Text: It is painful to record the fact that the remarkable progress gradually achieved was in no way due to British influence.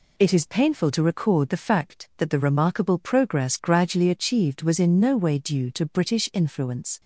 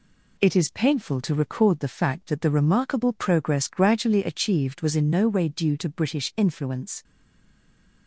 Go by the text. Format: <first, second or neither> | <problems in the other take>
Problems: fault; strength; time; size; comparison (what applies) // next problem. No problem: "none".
first | stays silent after the last word; from 7.0 s on; 1.0 s long